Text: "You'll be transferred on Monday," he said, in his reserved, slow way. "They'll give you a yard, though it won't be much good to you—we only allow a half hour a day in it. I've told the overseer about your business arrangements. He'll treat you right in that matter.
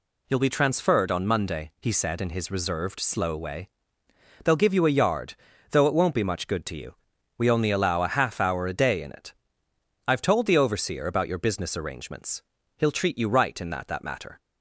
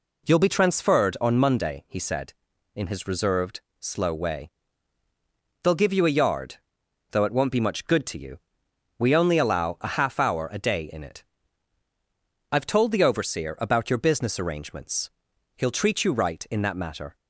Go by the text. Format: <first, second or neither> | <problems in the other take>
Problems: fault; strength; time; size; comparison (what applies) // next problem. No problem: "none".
second | says "that" twice; at 13.8 s